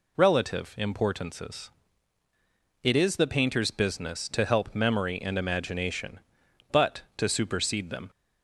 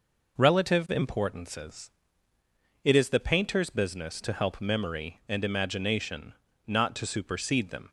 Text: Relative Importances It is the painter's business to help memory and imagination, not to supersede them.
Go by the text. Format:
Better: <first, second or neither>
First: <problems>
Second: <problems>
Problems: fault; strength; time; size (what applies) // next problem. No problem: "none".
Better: second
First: pauses between "Importances" and "It"; at 1.7 s; 1.1 s long // says "but" for "not"; at 6.7 s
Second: pauses between "Importances" and "It"; noticeable; at 1.8 s; 0.94 s long